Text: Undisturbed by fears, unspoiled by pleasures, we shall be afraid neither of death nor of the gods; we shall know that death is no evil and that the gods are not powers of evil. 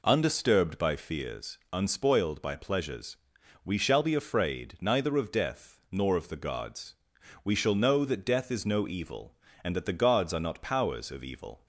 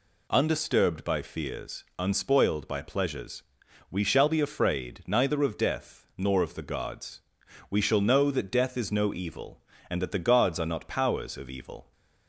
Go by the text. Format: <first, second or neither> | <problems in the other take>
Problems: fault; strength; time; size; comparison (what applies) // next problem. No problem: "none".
second | starts louder than the rest; until 1.1 s; 3.5 dB